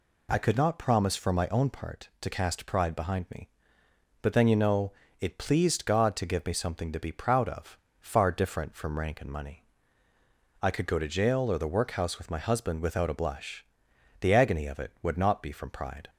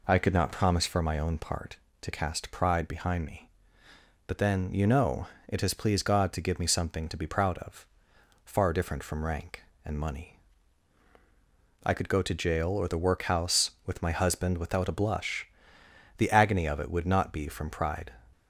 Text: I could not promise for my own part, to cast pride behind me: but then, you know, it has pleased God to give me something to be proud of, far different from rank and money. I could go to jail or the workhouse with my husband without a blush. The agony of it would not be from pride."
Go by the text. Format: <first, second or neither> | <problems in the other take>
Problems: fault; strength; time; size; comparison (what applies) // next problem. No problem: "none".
second | skips "has"; at 5.3 s